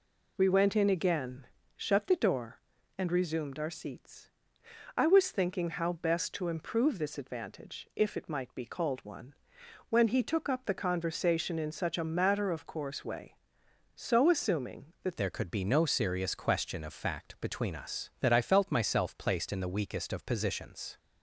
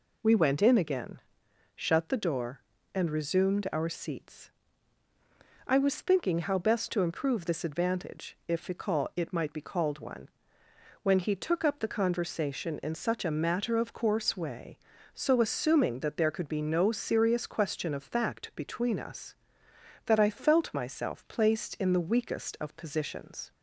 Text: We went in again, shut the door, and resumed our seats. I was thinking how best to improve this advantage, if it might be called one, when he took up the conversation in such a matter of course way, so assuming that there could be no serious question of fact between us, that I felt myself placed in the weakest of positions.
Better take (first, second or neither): second